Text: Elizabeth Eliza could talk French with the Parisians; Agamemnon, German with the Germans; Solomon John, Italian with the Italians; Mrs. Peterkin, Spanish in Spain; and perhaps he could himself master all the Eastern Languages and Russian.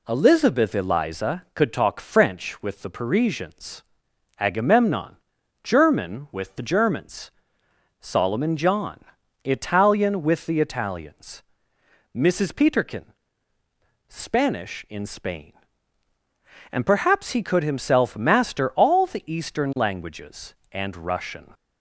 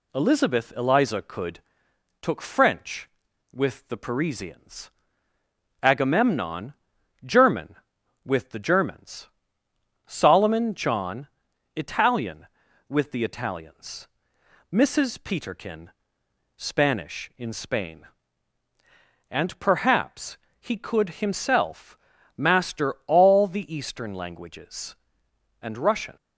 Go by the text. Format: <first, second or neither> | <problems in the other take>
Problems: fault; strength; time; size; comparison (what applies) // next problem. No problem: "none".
first | says "took" for "talk"; at 2.1 s // pauses between "perhaps" and "he"; slight; at 20.3 s; 0.22 s long // pauses between "himself" and "master"; at 21.9 s; 0.40 s long